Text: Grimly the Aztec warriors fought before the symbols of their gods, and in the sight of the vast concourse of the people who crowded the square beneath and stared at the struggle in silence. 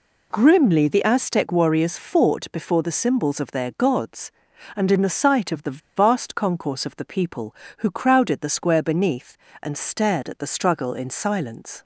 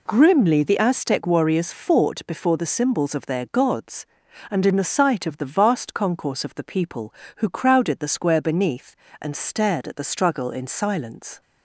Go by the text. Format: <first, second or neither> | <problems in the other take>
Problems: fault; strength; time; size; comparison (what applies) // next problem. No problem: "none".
second | pauses between "the" and "vast"; slight; at 5.7 s; 0.18 s long